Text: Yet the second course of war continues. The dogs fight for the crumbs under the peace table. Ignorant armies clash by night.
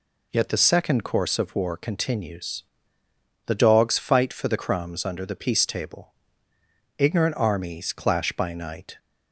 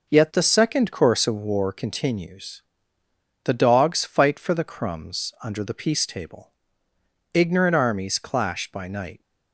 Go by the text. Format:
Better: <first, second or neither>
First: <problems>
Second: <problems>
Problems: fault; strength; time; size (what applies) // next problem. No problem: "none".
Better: first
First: none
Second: gets quieter; noticeable; throughout; 5.5 dB